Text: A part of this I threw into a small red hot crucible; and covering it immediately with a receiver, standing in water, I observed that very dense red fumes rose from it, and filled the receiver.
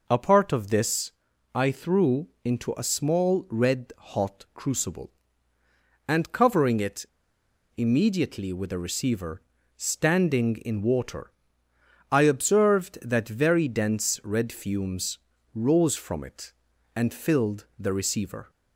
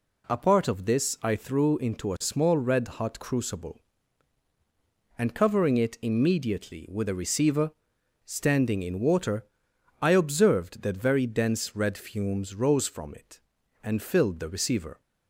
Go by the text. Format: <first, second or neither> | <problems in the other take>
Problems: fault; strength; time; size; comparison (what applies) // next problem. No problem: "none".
second | pauses between "this" and "I"; at 1.0 s; 0.42 s long // pauses between "threw" and "into"; slight; at 2.2 s; 0.16 s long // pauses between "it" and "immediately"; noticeable; at 7.0 s; 0.71 s long // pauses between "fumes" and "rose"; slight; at 15.1 s; 0.34 s long